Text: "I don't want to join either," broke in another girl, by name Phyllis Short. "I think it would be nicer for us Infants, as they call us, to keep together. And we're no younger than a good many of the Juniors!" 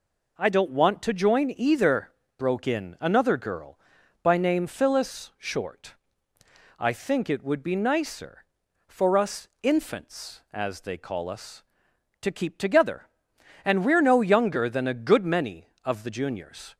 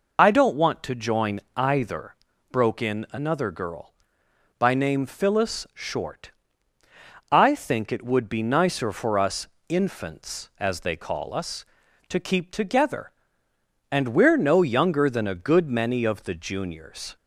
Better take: first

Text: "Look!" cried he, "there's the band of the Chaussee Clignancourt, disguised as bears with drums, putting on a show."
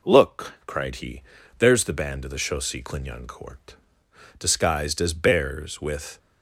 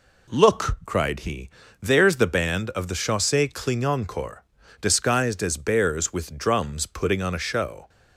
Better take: second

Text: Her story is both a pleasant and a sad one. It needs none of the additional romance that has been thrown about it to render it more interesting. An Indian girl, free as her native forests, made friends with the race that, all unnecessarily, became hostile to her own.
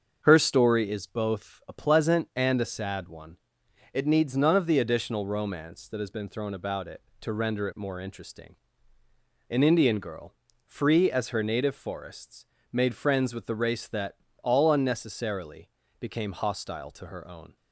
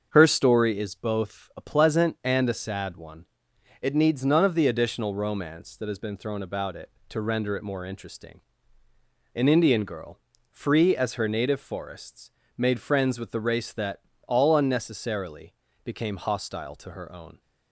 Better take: neither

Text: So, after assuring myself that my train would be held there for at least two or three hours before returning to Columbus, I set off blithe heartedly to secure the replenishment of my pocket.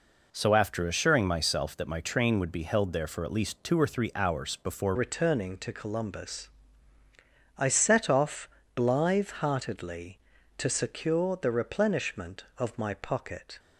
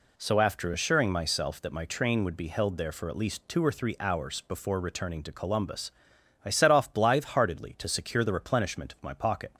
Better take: second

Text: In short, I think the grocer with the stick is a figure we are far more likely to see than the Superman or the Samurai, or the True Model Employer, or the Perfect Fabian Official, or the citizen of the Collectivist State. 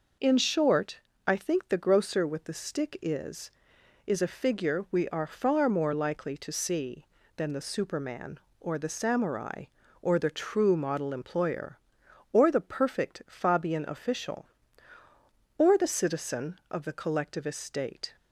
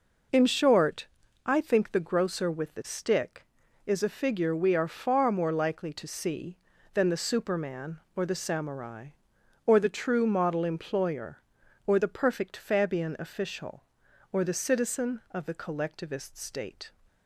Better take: second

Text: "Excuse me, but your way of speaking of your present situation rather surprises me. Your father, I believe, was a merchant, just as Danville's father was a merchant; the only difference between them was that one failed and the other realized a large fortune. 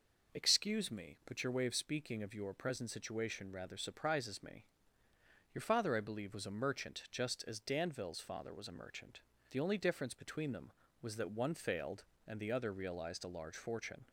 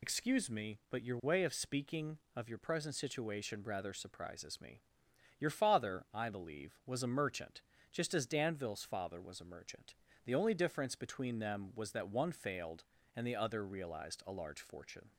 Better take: first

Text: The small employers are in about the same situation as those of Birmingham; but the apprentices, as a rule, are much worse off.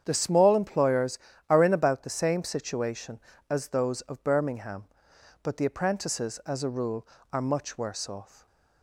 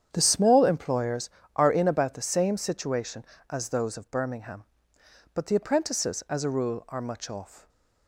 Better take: first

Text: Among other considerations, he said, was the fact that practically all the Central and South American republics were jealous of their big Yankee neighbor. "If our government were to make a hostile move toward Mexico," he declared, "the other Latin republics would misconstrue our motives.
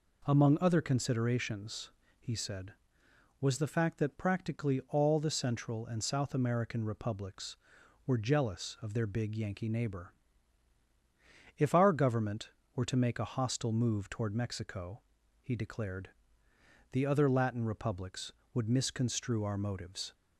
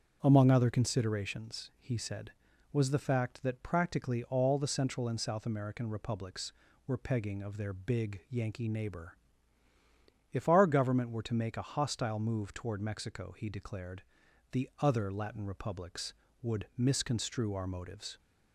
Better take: first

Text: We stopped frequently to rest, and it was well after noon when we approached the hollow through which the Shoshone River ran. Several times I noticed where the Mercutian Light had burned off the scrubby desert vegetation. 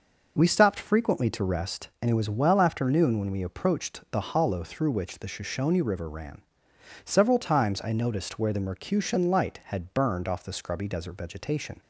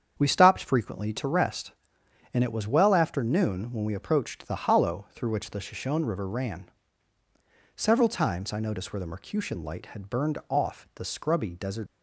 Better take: first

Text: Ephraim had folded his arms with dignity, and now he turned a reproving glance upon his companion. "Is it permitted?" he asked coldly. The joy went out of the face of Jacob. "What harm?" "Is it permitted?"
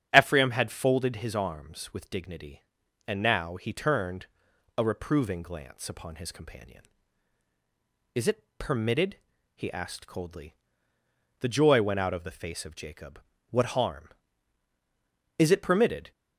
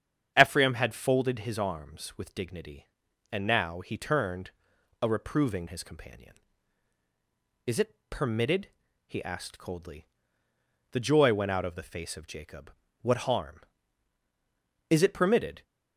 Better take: first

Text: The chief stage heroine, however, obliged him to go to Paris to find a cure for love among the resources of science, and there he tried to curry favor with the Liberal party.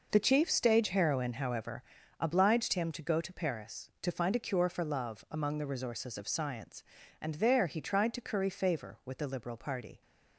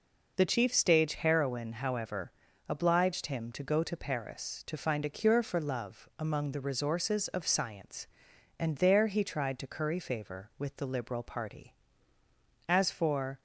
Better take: first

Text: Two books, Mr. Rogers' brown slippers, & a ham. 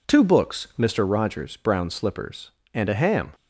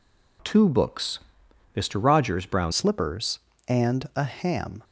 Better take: first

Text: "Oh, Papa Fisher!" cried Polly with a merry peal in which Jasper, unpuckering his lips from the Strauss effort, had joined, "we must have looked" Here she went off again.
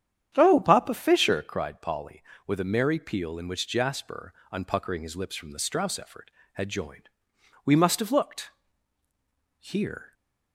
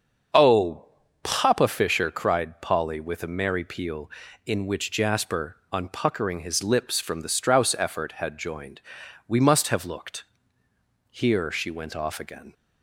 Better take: second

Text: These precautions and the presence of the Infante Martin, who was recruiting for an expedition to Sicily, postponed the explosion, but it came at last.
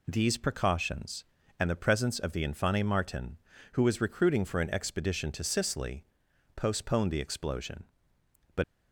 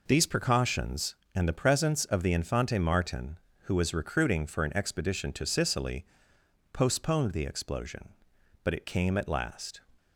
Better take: second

